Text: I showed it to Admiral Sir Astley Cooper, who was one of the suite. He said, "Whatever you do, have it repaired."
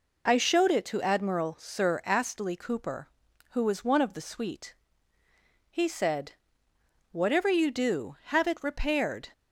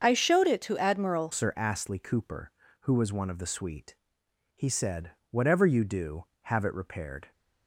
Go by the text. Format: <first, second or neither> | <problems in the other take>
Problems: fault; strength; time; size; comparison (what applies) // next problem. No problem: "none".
first | starts louder than the rest; until 1.0 s; 6.5 dB // changes voice at "Sir"; from 1.3 s on; 6.0 s long